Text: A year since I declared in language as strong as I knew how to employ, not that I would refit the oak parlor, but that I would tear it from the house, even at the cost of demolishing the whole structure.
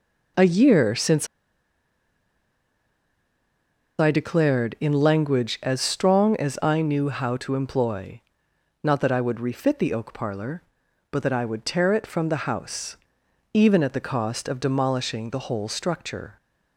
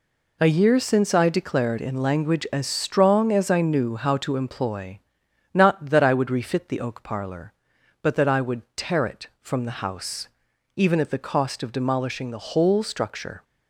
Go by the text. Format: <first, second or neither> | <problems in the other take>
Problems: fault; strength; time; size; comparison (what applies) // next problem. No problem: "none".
second | pauses between "since" and "I"; strong; at 1.2 s; 2.7 s long